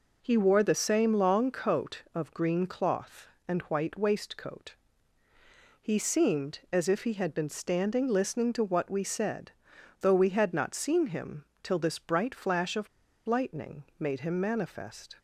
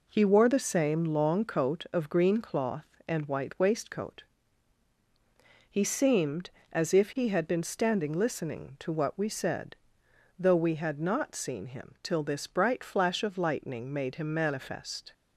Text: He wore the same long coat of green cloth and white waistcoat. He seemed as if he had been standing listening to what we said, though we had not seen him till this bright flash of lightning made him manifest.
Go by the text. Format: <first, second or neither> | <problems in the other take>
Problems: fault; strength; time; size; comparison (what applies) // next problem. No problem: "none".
second | pauses between "him" and "till"; slight; at 11.4 s; 0.18 s long // pauses between "of" and "lightning"; at 12.8 s; 0.40 s long // pauses between "lightning" and "made"; slight; at 13.8 s; 0.16 s long